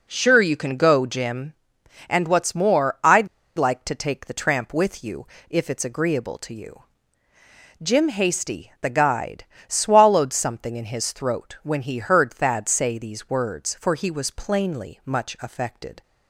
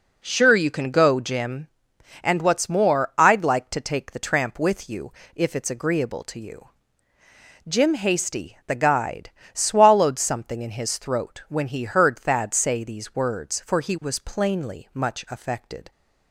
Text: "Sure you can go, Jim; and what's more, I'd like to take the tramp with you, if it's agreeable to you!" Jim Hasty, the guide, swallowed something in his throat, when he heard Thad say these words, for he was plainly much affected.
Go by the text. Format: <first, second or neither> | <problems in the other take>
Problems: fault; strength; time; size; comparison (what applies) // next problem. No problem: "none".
second | pauses between "I'd" and "like"; slight; at 3.2 s; 0.30 s long